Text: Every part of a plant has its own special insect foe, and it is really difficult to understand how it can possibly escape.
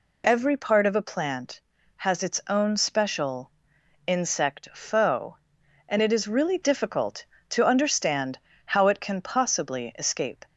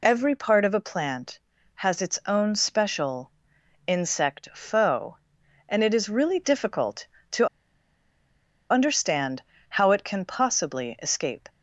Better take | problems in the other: first | pauses between "special" and "insect"; noticeable; at 3.3 s; 0.56 s long; noticeable in the first // pauses between "to" and "understand"; at 7.4 s; 1.2 s long // pauses between "understand" and "how"; slight; at 9.4 s; 0.26 s long; slight in the first

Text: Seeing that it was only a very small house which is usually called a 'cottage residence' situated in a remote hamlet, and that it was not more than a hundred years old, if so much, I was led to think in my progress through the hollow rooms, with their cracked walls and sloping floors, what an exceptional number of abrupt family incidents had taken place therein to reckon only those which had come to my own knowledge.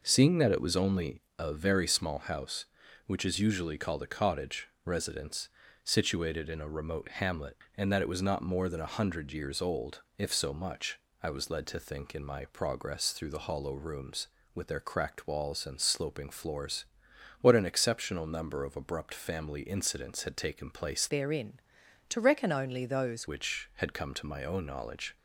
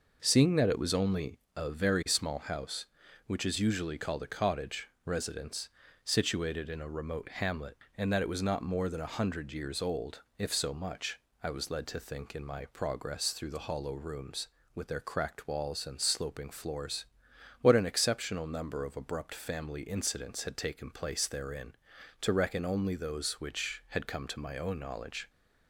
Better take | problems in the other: second | pauses between "only" and "a"; slight; at 1.2 s; 0.18 s long; slight in the second // pauses between "cottage" and "residence"; slight; at 4.6 s; 0.16 s long; slight in the second // pauses between "residence" and "situated"; at 5.4 s; 0.38 s long; also in the second // changes voice from "therein" to "those"; from 21.0 to 23.2 s; 2.2 s long

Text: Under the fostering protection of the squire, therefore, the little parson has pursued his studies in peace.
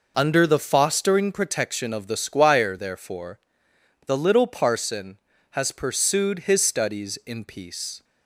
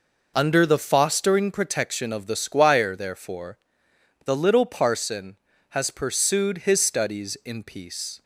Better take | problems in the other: neither | none

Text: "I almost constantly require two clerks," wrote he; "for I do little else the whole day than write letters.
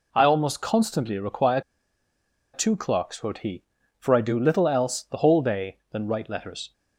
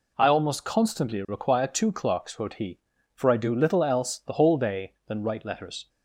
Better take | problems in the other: second | pauses between "require" and "two"; noticeable; at 1.5 s; 0.93 s long

